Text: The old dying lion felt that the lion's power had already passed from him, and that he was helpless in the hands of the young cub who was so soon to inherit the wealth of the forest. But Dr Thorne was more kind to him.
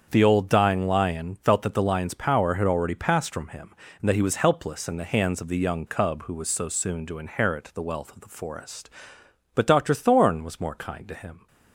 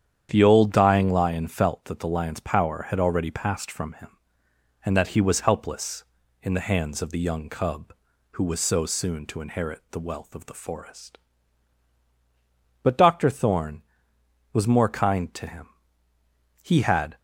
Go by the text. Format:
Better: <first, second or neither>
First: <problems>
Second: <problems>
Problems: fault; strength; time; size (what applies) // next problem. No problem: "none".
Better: first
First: starts louder than the rest; strong; until 1.1 s; 7 dB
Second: starts louder than the rest; strong; until 1.3 s; 9 dB // goes on to say "He had"; from 16.6 s on; 0.55 s long